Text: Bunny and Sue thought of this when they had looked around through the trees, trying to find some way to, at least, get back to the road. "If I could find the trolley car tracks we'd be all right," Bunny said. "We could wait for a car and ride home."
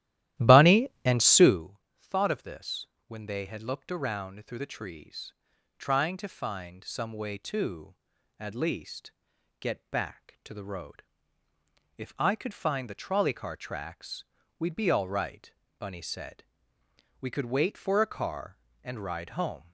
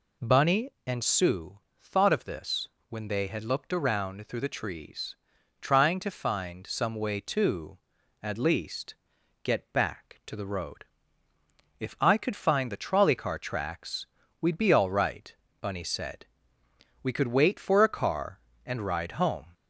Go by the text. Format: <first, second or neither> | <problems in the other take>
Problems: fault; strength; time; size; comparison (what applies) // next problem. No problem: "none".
second | starts louder than the rest; strong; until 1.7 s; 13.5 dB // pauses between "Sue" and "thought"; slight; at 1.7 s; 0.20 s long; slight in the second // pauses between "this" and "when"; slight; at 2.8 s; 0.22 s long; slight in the second // pauses between "tracks" and "we'd"; slight; at 14.2 s; 0.34 s long; slight in the second